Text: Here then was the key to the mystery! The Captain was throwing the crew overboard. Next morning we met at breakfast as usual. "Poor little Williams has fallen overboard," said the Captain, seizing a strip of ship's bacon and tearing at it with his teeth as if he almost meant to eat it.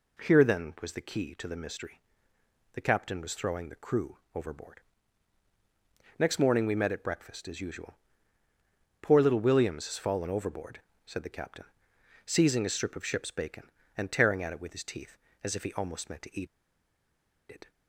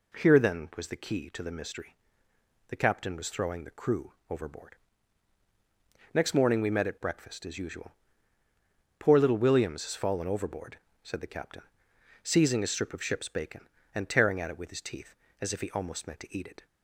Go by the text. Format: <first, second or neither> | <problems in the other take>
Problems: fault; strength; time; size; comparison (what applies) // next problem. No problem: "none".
second | pauses between "crew" and "overboard"; slight; at 4.1 s; 0.16 s long; slight in the second // pauses between "eat" and "it"; at 16.4 s; 1.0 s long